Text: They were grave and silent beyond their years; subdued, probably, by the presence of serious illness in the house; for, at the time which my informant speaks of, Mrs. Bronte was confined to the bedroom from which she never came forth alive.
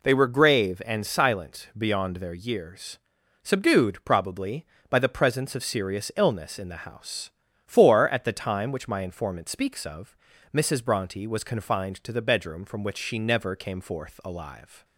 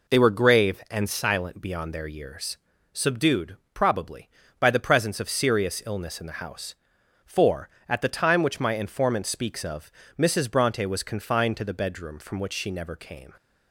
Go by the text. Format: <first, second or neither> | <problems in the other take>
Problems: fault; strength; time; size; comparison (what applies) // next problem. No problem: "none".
first | stops before "forth alive"; at 13.3 s